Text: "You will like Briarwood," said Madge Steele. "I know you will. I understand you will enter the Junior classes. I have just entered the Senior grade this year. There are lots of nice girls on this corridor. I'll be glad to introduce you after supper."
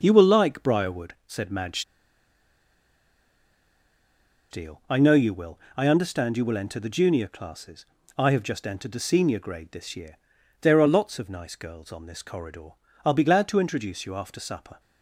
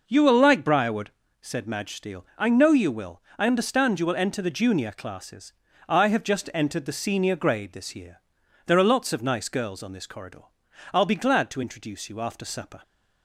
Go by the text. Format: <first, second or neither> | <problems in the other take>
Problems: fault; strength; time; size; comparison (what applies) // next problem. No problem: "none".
second | starts louder than the rest; until 1.0 s; 6.5 dB // pauses between "Madge" and "Steele"; strong; at 1.8 s; 2.6 s long